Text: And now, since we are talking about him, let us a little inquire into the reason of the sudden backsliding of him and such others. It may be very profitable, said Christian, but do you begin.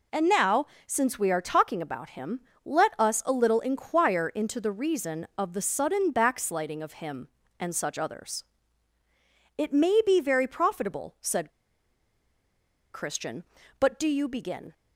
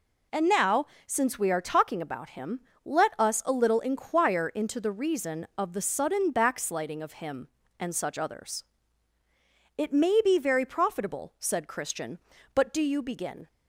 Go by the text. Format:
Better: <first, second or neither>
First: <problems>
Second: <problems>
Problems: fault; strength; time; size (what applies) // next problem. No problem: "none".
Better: second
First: pauses between "said" and "Christian"; strong; at 11.4 s; 1.4 s long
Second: none